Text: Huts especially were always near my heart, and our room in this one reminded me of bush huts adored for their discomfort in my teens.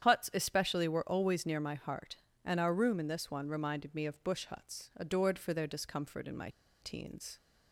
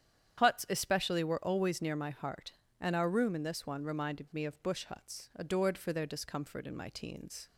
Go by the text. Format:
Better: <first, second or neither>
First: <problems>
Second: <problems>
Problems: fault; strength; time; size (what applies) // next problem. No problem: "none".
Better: second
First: starts louder than the rest; strong; until 1.0 s; 9 dB // pauses between "my" and "teens"; slight; at 6.4 s; 0.32 s long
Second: starts louder than the rest; strong; until 1.4 s; 9 dB